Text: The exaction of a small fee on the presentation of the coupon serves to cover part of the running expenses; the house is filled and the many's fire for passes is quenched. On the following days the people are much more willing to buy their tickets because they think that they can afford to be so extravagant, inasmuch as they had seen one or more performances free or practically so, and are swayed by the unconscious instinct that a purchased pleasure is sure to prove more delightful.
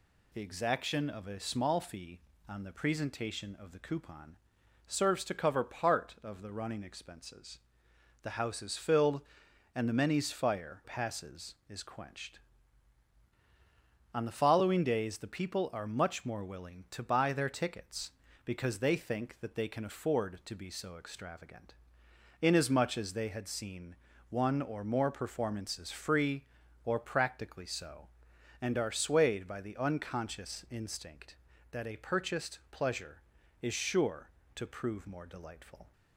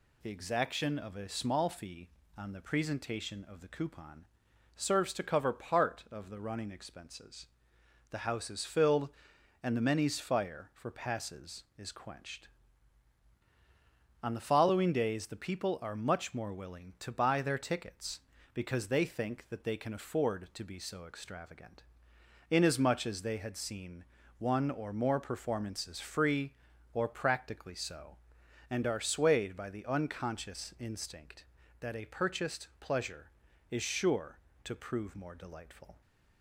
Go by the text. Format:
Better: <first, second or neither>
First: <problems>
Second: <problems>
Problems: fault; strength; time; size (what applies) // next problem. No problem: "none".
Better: second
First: pauses between "coupon" and "serves"; noticeable; at 4.3 s; 0.50 s long // skips "for"; at 10.8 s // pauses between "seen" and "one"; slight; at 23.9 s; 0.32 s long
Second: pauses between "coupon" and "serves"; noticeable; at 4.2 s; 0.50 s long // pauses between "seen" and "one"; slight; at 24.0 s; 0.32 s long